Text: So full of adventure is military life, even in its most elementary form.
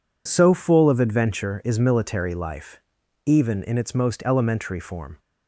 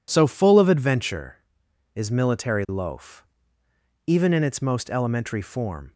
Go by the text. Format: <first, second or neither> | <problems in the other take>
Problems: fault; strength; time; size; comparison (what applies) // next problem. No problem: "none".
first | says "loaf" for "life"; at 2.6 s